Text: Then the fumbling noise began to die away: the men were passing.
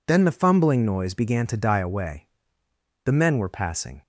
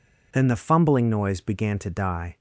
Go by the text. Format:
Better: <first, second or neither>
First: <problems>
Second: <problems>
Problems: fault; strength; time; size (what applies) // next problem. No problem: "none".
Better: first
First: none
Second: stops before "away the men were passing"; at 2.3 s